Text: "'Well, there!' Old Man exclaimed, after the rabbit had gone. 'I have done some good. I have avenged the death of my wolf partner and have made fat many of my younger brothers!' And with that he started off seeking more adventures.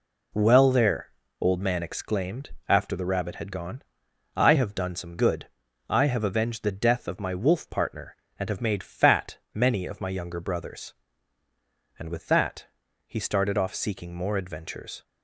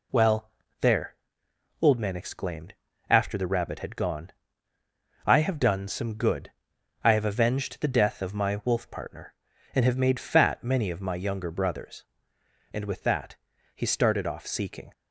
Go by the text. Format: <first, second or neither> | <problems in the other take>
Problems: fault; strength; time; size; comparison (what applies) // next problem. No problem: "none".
first | pauses between "that" and "he"; at 13.3 s; 0.38 s long; also in the first // stops before "more adventures"; at 14.9 s